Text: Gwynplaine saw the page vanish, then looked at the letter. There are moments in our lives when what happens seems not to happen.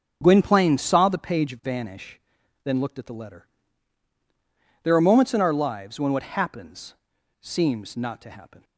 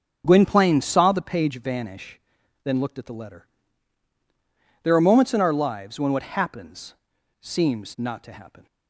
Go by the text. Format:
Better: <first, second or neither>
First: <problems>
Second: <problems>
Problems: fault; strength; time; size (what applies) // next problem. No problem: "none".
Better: neither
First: starts louder than the rest; strong; until 1.2 s; 7.5 dB // pauses between "happens" and "seems"; at 6.9 s; 0.44 s long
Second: starts louder than the rest; until 1.2 s; 7 dB // pauses between "happens" and "seems"; at 6.9 s; 0.44 s long